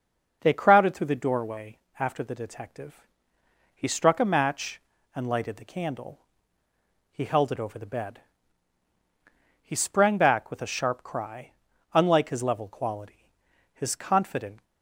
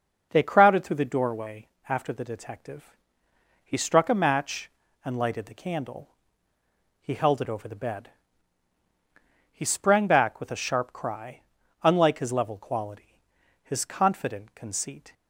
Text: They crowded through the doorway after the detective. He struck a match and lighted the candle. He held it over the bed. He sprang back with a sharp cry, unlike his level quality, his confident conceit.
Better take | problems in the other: second | pauses between "doorway" and "after"; slight; at 1.7 s; 0.20 s long; slight in the second // stops before "conceit"; at 14.6 s

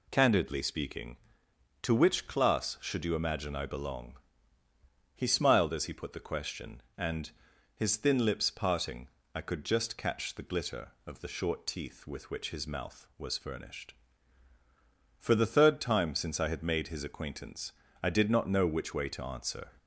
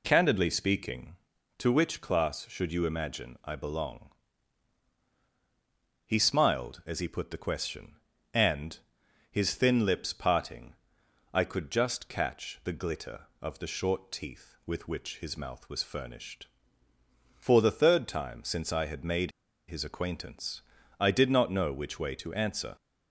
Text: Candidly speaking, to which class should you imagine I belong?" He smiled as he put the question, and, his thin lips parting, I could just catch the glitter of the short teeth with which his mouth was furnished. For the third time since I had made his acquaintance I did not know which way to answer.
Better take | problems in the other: first | pauses between "made" and "his"; at 19.3 s; 0.37 s long // pauses between "acquaintance" and "I"; at 20.6 s; 0.38 s long; slight in the first

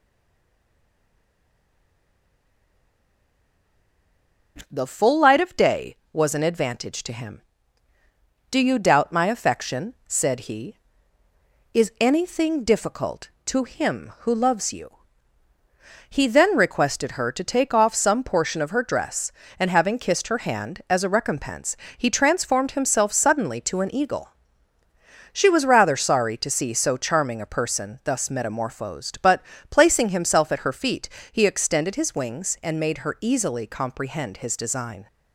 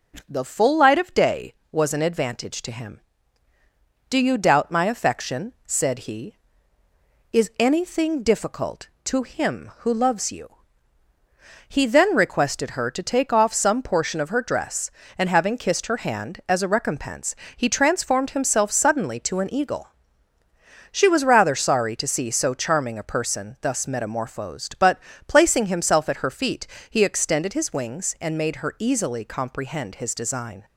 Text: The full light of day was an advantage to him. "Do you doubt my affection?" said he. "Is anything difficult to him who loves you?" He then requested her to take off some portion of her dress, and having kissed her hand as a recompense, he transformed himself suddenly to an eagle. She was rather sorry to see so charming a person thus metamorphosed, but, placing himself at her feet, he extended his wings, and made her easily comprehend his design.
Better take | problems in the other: second | stays silent before the first word; strong; until 4.5 s; 4.5 s long

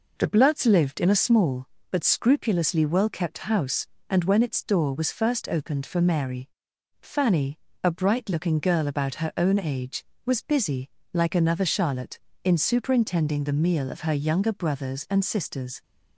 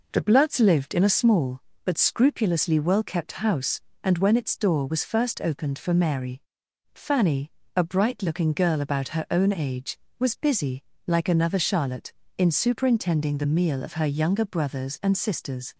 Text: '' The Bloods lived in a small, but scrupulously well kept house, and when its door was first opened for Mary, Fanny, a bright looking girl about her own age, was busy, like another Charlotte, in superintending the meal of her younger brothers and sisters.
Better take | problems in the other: neither | none

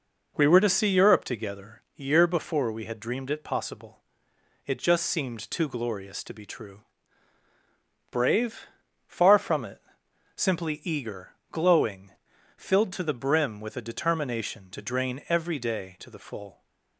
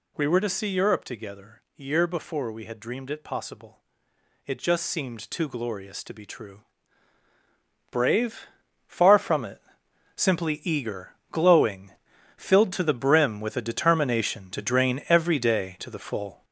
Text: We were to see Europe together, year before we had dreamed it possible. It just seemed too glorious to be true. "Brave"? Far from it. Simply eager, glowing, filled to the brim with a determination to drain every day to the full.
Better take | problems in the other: first | gets louder; noticeable; throughout; 5.5 dB

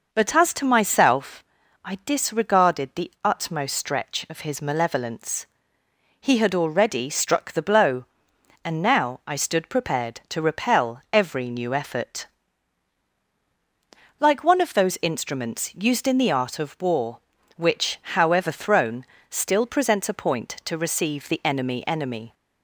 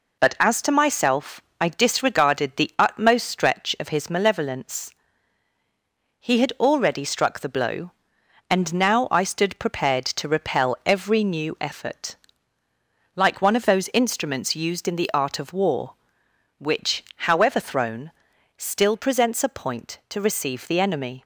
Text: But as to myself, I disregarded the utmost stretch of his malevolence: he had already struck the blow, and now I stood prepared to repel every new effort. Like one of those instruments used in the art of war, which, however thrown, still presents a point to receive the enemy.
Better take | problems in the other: second | says "enemy" twice; at 21.8 s

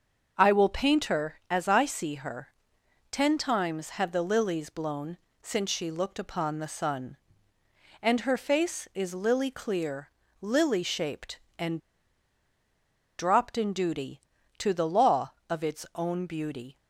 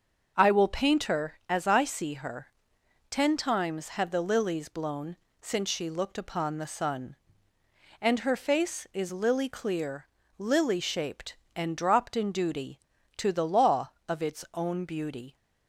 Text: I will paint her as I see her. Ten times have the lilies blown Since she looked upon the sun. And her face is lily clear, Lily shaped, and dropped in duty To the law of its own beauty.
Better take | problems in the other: second | starts louder than the rest; until 1.3 s; 6.5 dB; also in the second // pauses between "blown" and "Since"; slight; at 5.1 s; 0.24 s long; slight in the second // pauses between "and" and "dropped"; strong; at 11.7 s; 1.4 s long

